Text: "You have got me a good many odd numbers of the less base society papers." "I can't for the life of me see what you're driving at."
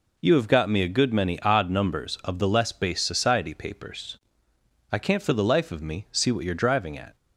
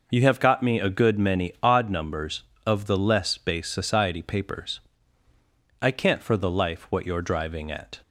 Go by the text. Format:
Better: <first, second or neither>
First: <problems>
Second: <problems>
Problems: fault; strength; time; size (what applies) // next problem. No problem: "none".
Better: first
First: none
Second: skips "of me see"; at 6.8 s